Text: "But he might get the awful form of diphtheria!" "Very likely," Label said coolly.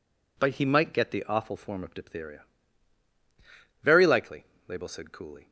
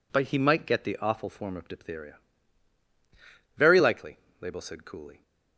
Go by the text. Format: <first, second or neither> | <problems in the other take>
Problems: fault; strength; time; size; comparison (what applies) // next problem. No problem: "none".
neither | none